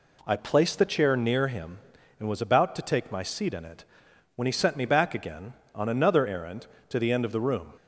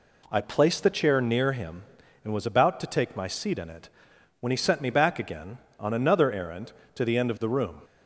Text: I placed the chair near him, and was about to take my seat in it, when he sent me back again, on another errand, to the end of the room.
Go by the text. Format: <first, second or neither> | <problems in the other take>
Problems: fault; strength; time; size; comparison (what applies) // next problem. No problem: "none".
neither | none